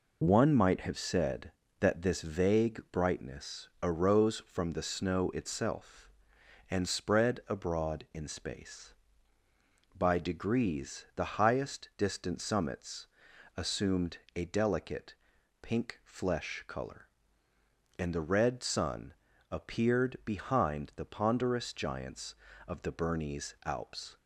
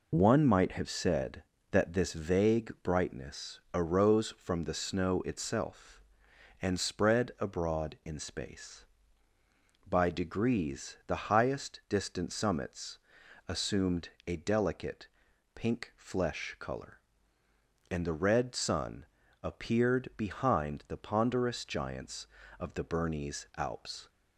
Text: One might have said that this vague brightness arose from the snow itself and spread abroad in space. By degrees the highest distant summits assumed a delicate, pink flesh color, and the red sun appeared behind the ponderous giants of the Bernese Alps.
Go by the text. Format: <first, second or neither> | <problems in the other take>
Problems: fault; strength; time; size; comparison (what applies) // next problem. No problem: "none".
neither | pauses between "brightness" and "arose"; slight; the same in both // pauses between "summits" and "assumed"; noticeable; the same in both // pauses between "assumed" and "a"; slight; the same in both // pauses between "sun" and "appeared"; slight; the same in both